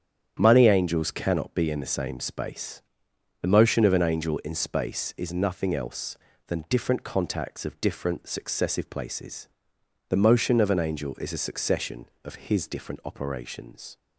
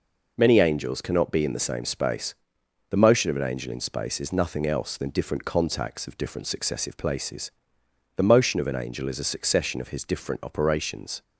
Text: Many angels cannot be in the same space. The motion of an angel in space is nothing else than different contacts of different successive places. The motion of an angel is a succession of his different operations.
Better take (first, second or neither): second